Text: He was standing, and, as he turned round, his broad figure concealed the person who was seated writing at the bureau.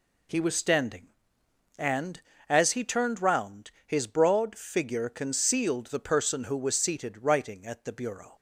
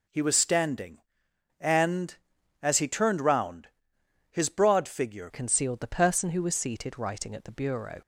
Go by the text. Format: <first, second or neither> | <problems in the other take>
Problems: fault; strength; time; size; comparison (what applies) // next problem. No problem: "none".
first | changes voice at "concealed"; from 5.3 s on; 2.7 s long